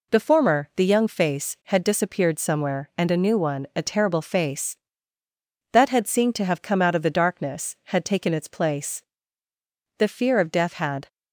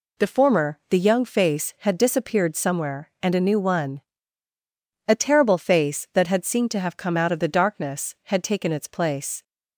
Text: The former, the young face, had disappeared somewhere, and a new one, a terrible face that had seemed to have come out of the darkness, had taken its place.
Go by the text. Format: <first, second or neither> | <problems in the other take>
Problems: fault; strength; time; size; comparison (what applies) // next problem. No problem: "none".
second | goes on to say "The fear of death had"; noticeable; from 9.9 s on; 1.1 s long